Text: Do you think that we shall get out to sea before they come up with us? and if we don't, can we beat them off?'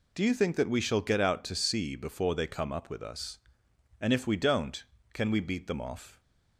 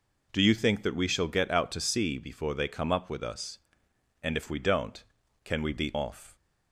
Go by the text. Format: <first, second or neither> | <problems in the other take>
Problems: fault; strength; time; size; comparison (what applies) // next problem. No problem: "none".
first | skips "them"; at 5.9 s